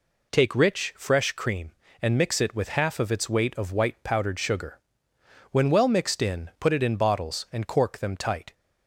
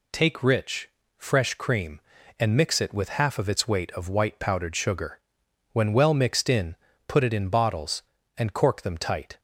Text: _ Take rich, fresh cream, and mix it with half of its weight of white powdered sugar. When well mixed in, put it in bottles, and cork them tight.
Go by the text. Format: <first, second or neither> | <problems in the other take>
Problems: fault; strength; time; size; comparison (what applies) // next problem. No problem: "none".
neither | none